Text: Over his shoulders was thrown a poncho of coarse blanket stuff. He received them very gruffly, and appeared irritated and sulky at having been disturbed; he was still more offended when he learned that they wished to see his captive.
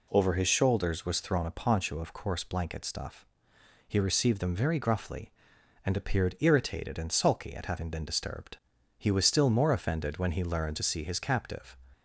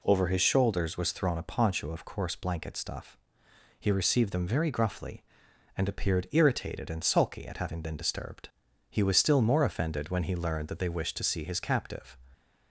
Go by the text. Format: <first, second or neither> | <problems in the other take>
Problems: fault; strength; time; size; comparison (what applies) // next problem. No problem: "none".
second | skips "that they wished"; at 10.7 s